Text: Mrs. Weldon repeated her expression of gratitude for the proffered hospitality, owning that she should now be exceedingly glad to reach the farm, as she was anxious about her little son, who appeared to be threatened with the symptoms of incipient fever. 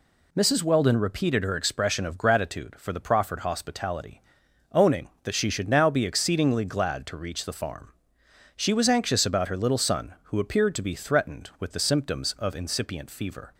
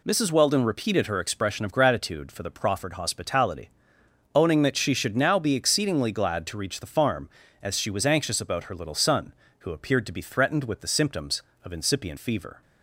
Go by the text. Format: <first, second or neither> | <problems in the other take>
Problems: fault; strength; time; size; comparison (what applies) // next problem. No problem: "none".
second | skips "as"; at 8.2 s